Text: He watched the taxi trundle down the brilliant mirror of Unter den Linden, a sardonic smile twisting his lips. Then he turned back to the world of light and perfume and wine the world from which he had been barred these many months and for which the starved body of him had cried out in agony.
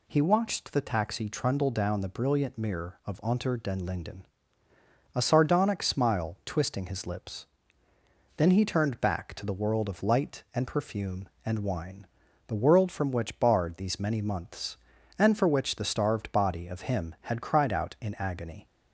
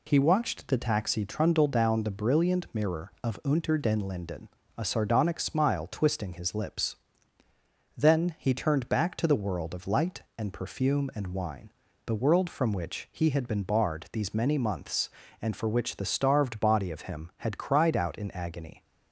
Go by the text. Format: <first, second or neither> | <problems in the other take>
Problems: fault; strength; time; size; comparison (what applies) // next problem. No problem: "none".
second | pauses between "wine" and "the"; at 12.0 s; 0.42 s long; slight in the second // skips "he had been"; at 13.3 s